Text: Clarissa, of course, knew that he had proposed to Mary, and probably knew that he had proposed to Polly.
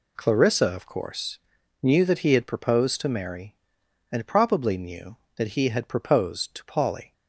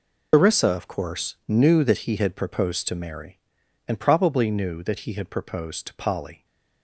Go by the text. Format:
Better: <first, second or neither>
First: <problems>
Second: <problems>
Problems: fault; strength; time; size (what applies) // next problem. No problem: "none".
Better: first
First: none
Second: loses the start of "Clarissa"; at 0.3 s; 140 ms